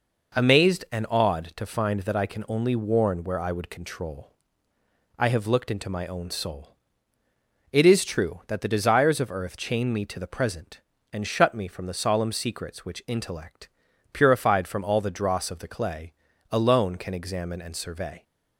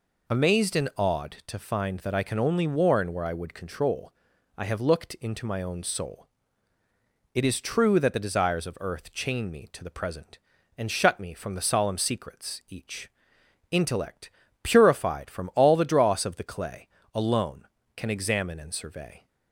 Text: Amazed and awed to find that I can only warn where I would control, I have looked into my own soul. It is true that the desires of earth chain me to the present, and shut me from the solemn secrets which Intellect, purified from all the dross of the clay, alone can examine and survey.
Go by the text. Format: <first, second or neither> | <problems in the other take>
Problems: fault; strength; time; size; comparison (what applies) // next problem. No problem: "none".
first | says "each" for "which"; at 12.6 s